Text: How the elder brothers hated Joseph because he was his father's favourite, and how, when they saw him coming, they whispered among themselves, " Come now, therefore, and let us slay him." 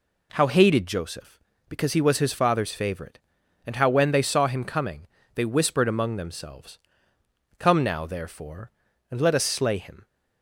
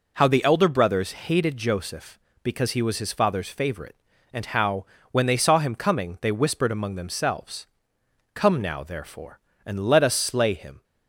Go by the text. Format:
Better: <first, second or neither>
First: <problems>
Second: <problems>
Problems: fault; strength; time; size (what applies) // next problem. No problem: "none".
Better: second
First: skips "the elder brothers"; at 0.4 s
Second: none